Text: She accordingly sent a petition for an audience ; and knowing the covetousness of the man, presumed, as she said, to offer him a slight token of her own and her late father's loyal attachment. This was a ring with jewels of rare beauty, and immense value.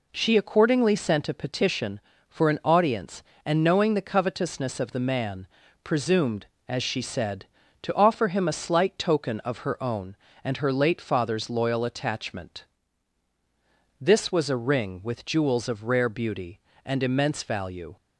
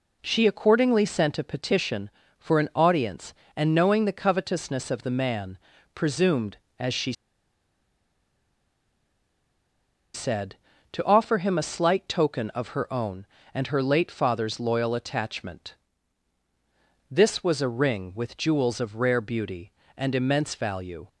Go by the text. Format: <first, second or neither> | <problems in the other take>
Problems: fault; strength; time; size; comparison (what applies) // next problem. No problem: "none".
first | pauses between "she" and "said"; strong; at 7.1 s; 3.0 s long